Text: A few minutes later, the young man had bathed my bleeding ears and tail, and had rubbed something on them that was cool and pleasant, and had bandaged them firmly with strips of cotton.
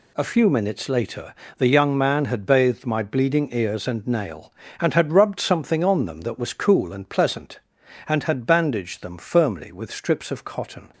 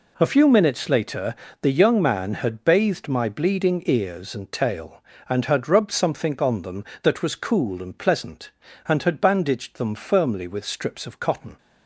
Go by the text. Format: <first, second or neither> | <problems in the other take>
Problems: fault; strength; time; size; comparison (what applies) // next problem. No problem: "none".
second | says "nail" for "tail"; at 4.0 s